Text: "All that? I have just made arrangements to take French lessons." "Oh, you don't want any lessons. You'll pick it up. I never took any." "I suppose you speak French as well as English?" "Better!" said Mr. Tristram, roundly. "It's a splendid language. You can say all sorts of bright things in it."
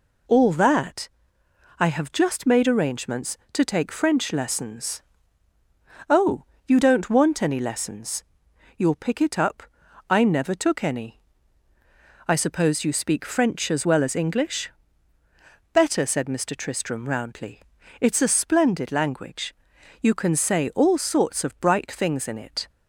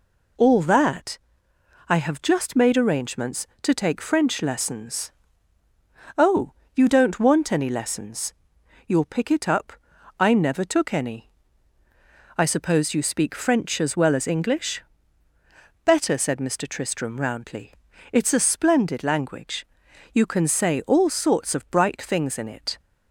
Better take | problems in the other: neither | none

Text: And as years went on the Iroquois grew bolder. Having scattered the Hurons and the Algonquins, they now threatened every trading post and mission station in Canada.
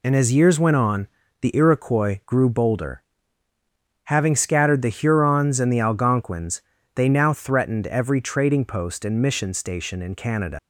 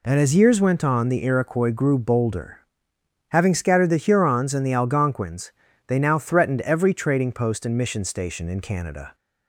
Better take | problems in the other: second | pauses between "on" and "the"; slight; at 1.0 s; 0.34 s long // leaves "Canada" unfinished; at 10.5 s; 110 ms

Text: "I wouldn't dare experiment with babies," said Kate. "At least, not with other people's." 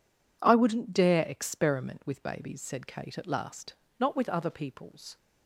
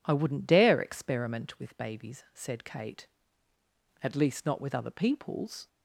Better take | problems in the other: second | says "last" for "least"; at 3.2 s

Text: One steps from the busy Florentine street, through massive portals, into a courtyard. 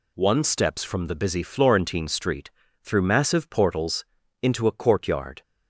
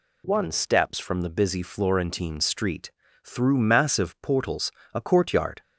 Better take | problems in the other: first | skips "into"; at 4.8 s

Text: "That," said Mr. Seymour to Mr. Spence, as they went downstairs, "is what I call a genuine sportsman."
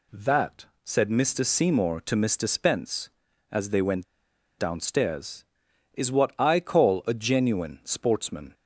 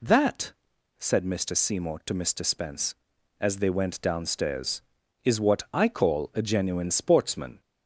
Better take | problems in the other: second | pauses between "went" and "downstairs"; noticeable; at 4.0 s; 0.54 s long

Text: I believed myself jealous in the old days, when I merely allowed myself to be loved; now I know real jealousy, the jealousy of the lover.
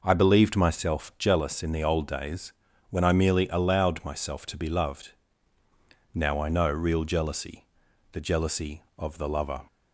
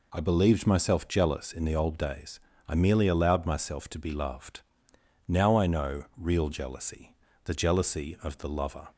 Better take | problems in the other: first | skips "when"; at 2.5 s

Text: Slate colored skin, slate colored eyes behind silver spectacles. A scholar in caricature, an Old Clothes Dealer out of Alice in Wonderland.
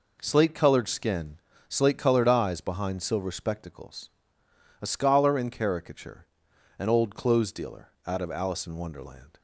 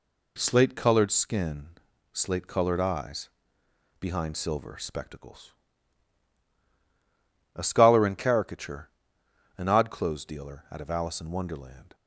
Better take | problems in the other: first | pauses between "eyes" and "behind"; noticeable; at 3.2 s; 0.70 s long // says "Odd" for "Old"; at 9.6 s

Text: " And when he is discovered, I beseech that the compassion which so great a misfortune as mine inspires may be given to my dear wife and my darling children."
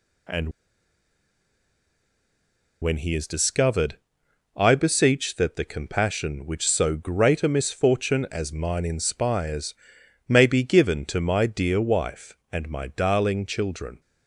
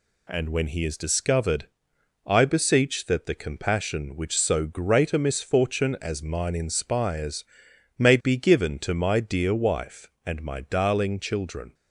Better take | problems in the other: second | pauses between "And" and "when"; strong; at 0.4 s; 2.3 s long // pauses between "inspires" and "may"; noticeable; at 9.7 s; 0.54 s long; noticeable in the second

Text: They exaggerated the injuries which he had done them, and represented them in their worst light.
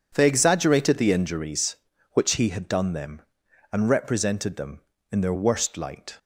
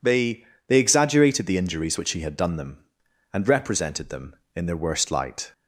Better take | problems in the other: first | says "They" twice; at 0.6 s

